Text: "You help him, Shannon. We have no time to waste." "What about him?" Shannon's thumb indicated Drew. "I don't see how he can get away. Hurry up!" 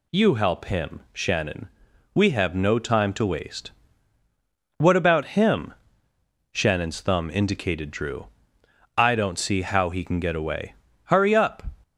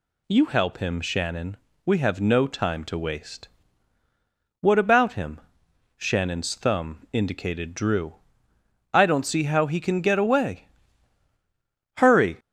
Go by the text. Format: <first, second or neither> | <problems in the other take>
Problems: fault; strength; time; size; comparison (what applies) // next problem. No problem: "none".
first | stops before "up"; at 12.3 s